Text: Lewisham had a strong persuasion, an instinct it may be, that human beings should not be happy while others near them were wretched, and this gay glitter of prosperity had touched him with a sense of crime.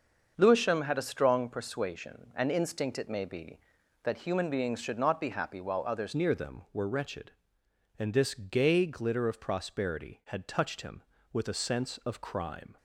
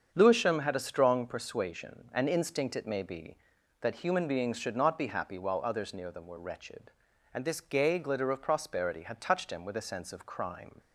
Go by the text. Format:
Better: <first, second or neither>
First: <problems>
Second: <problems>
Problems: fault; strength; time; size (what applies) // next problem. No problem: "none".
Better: second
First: starts louder than the rest; until 1.3 s; 6.5 dB // changes voice at "near"; from 6.1 s on; 6.6 s long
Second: starts louder than the rest; strong; until 1.1 s; 7.5 dB